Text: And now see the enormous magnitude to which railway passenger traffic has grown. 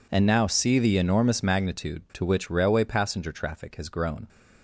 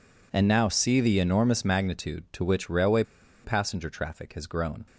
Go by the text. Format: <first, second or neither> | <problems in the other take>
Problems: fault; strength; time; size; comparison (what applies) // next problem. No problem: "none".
first | pauses between "railway" and "passenger"; at 3.0 s; 0.40 s long